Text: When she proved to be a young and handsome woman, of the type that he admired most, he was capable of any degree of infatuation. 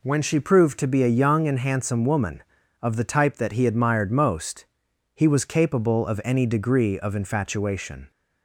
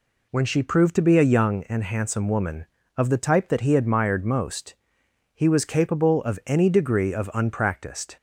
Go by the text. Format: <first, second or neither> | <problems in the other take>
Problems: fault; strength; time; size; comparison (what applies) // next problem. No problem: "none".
first | says "unpracticed" for "infatuation"; at 7.3 s